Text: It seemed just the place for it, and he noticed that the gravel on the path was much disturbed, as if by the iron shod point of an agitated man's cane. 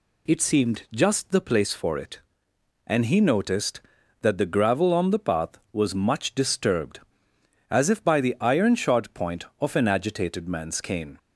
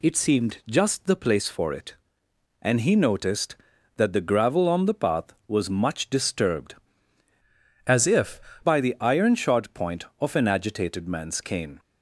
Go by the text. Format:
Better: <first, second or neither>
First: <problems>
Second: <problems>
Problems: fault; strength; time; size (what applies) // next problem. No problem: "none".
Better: first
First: none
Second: changes voice from "as" to "if"; from 7.8 to 8.3 s; 0.5 s long